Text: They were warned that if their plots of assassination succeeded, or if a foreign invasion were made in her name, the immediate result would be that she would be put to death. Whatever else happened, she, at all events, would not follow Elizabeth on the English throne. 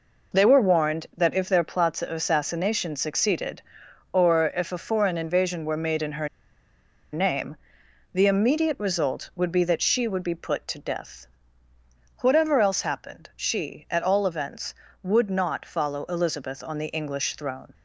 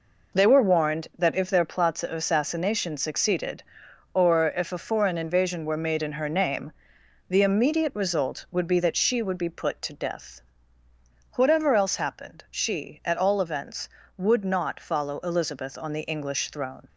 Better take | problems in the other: second | pauses between "her" and "name"; noticeable; at 6.2 s; 0.86 s long

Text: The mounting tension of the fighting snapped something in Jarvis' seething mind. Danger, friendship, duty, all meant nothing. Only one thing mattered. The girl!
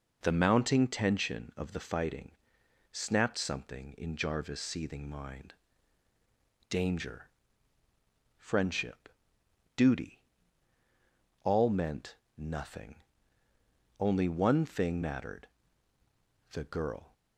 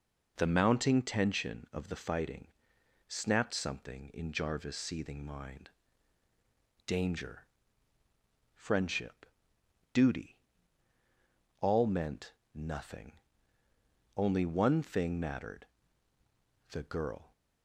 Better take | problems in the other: neither | pauses between "fighting" and "snapped"; noticeable; the same in both // pauses between "meant" and "nothing"; slight; the same in both

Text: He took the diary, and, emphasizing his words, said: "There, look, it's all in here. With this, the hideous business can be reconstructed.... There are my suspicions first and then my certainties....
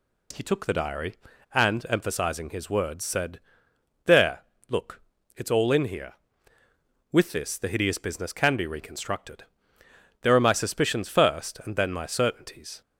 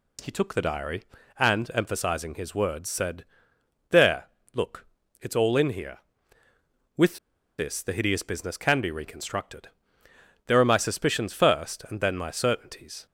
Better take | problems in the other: first | pauses between "With" and "this"; at 7.1 s; 0.42 s long

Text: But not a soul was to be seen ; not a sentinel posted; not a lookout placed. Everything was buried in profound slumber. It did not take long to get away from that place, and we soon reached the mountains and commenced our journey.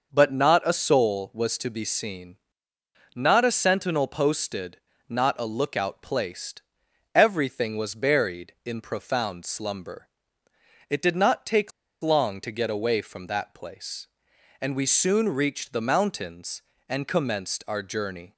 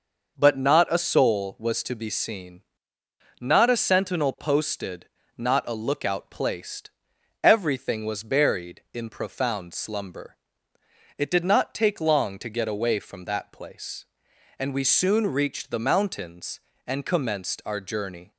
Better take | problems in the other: second | starts louder than the rest; noticeable; until 1.1 s; 6 dB // pauses between "take" and "long"; slight; at 11.7 s; 0.31 s long

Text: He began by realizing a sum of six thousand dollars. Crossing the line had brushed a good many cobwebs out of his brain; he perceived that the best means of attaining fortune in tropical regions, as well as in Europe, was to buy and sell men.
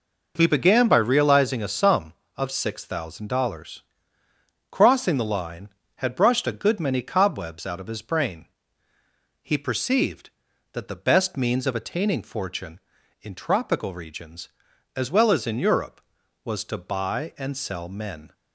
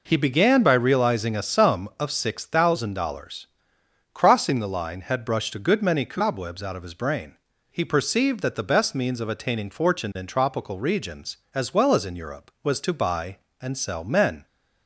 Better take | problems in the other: neither | none

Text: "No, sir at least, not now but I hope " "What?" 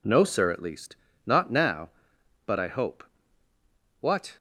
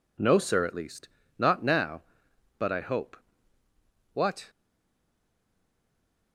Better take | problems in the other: first | stays silent after the last word; noticeable; from 4.4 s on; 1.9 s long

